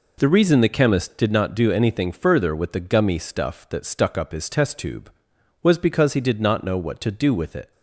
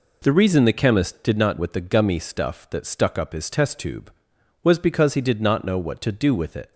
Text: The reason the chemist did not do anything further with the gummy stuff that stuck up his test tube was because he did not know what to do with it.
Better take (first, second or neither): first